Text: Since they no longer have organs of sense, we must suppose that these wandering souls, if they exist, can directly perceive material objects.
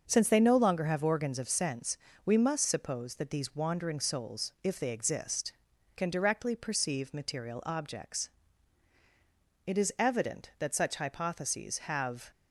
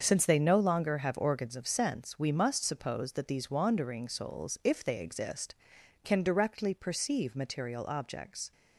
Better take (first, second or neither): second